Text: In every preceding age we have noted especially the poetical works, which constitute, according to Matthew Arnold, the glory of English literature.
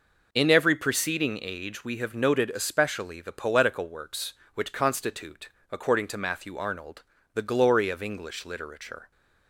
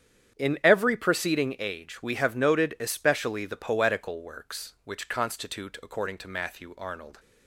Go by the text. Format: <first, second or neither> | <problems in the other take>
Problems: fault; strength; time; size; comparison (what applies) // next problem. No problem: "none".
first | starts louder than the rest; strong; until 1.4 s; 9 dB // stops before "the glory of English literature"; at 7.1 s